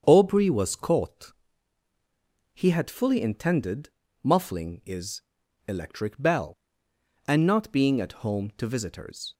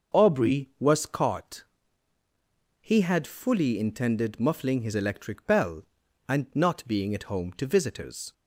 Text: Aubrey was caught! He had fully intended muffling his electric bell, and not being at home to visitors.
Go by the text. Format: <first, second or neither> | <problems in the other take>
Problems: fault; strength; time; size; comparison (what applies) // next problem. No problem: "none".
second | starts louder than the rest; strong; until 1.0 s; 7.5 dB // pauses between "intended" and "muffling"; slight; at 3.8 s; 0.34 s long // says "is" for "his"; at 4.8 s